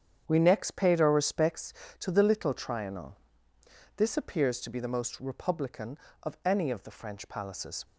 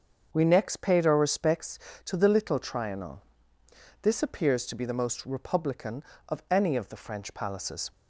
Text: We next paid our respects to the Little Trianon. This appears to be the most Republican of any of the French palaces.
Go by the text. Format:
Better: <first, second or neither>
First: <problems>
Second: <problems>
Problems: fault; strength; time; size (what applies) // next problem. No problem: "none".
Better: second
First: gets quieter; strong; throughout; 10.5 dB // starts louder than the rest; strong; until 1.2 s; 8 dB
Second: starts louder than the rest; until 1.3 s; 6.5 dB